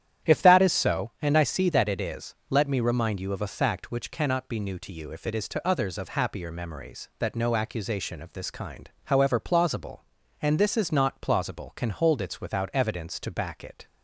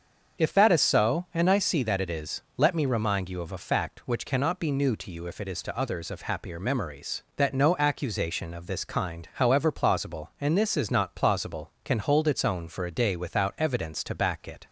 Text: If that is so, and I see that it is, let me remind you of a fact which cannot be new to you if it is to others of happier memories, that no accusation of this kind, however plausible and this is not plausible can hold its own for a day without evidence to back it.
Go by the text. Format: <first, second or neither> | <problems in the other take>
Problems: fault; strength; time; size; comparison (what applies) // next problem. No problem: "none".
second | starts louder than the rest; strong; until 1.3 s; 10.5 dB; also in the second // skips "own for a day"; at 12.3 s